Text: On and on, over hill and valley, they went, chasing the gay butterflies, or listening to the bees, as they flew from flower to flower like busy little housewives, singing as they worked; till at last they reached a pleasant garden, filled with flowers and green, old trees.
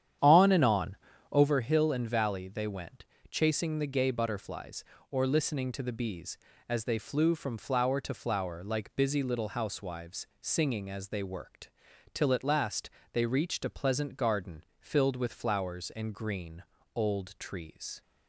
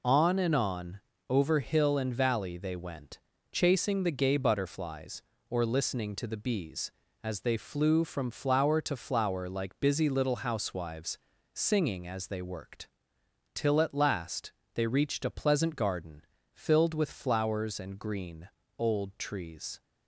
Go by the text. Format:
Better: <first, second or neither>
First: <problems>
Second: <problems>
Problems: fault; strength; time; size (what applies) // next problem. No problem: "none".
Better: second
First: starts louder than the rest; strong; until 1.5 s; 9.5 dB // pauses between "last" and "they"; slight; at 12.8 s; 0.24 s long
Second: pauses between "last" and "they"; slight; at 14.5 s; 0.22 s long